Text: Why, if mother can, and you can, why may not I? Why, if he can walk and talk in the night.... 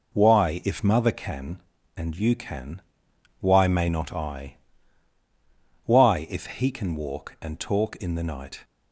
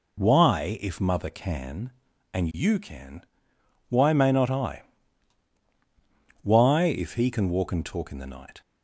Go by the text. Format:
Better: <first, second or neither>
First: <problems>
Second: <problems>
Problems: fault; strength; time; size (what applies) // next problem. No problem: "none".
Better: neither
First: none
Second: none